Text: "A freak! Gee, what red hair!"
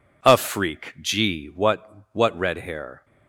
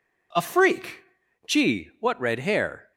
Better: second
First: says "what" twice; at 2.1 s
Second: none

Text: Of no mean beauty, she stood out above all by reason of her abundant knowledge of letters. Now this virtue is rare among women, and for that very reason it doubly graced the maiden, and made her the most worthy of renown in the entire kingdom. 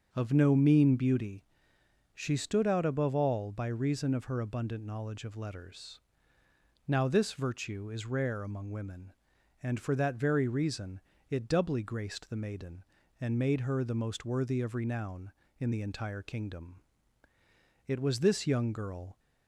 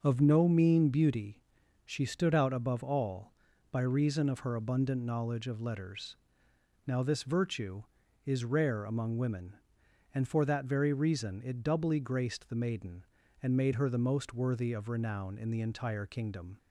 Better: second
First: starts louder than the rest; until 1.1 s; 6.5 dB // pauses between "reason" and "it"; slight; at 10.9 s; 0.30 s long // goes on to say "It was this young girl"; from 17.8 s on; 1.3 s long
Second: none

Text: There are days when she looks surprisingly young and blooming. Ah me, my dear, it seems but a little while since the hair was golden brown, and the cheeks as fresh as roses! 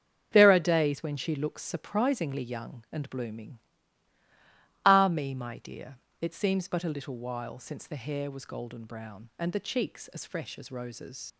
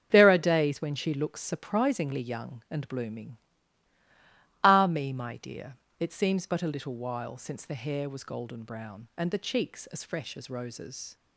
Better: second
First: starts louder than the rest; strong; until 1.3 s; 7.5 dB // leaves "roses" unfinished; at 11.3 s; 65 ms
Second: starts louder than the rest; strong; until 1.1 s; 7.5 dB

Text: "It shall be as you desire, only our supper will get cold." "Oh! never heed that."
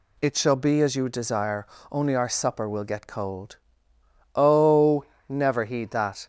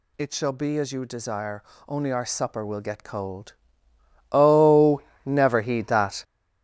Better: first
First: none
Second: gets louder; strong; throughout; 10 dB

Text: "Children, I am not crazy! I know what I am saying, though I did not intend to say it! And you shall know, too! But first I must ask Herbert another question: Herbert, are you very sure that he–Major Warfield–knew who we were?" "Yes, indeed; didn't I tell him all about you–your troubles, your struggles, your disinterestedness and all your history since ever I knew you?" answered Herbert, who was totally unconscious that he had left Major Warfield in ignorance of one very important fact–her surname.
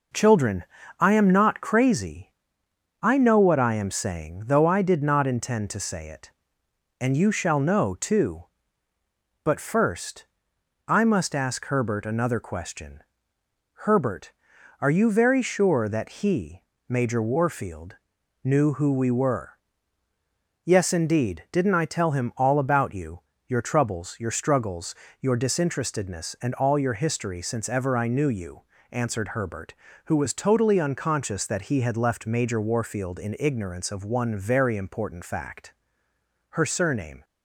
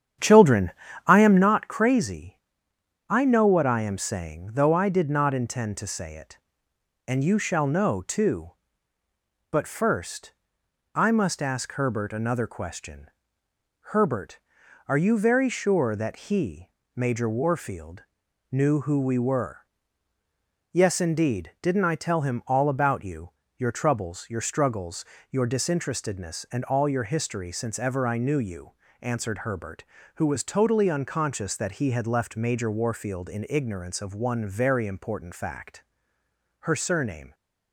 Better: first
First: pauses between "first" and "I"; noticeable; at 10.2 s; 0.60 s long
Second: starts louder than the rest; strong; until 1.5 s; 9.5 dB // pauses between "first" and "I"; noticeable; at 10.3 s; 0.60 s long

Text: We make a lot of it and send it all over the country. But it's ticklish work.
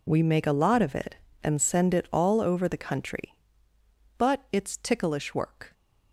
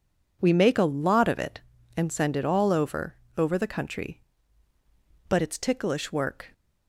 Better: first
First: none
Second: says "over" twice; at 3.3 s

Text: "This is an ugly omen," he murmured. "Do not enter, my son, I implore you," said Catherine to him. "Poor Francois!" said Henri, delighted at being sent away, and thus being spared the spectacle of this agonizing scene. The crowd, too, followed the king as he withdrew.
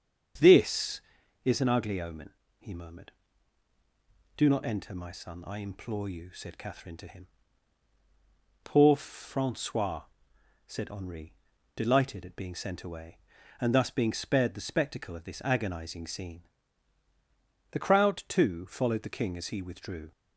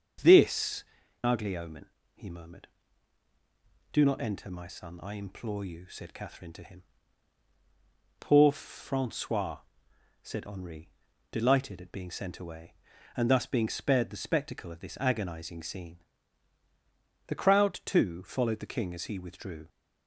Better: first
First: starts louder than the rest; strong; until 1.8 s; 7.5 dB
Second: starts louder than the rest; strong; until 1.6 s; 7 dB // skips "is an"; at 1.0 s

